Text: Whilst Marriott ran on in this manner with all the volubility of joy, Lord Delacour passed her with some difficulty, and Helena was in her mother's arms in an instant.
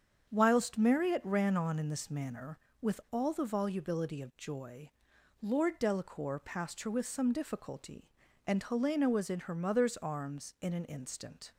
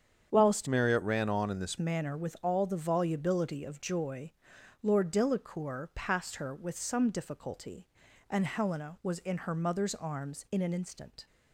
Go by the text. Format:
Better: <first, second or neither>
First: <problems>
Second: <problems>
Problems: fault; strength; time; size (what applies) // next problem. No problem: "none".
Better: first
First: starts louder than the rest; strong; until 1.3 s; 7.5 dB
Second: starts louder than the rest; strong; until 1.3 s; 8 dB // changes voice from "Marriott" to "this"; from 0.6 to 1.7 s; 1.1 s long